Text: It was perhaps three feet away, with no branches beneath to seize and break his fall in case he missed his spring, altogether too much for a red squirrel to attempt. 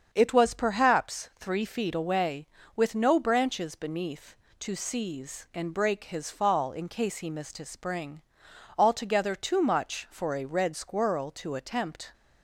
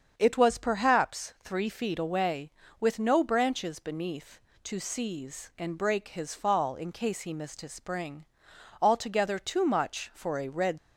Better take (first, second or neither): first